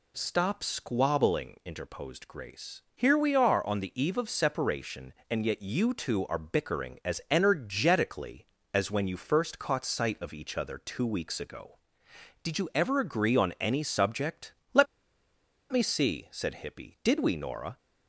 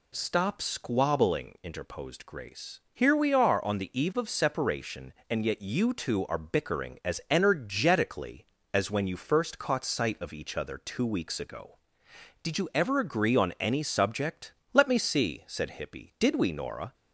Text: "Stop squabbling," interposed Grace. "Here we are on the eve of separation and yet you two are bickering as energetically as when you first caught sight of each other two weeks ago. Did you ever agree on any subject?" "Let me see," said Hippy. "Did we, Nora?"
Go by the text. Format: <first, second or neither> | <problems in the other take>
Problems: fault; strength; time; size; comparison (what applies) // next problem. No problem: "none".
second | pauses between "Let" and "me"; noticeable; at 14.8 s; 0.85 s long